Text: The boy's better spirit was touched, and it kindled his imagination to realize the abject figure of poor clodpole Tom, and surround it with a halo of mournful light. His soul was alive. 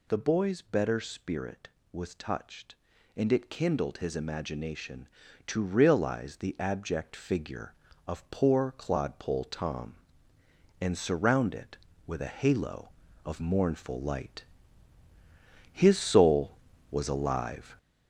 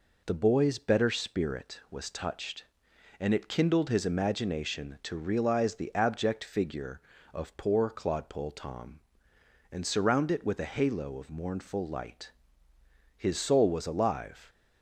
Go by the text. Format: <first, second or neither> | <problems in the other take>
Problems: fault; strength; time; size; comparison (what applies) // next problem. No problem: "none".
second | gets louder; noticeable; throughout; 5.5 dB